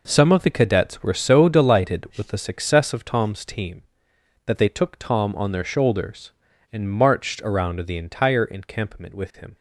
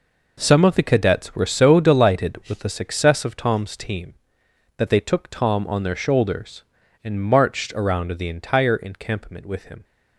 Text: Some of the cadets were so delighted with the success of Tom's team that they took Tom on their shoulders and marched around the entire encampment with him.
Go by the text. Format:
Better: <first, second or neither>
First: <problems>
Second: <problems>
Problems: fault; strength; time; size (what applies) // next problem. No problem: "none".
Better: neither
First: none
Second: none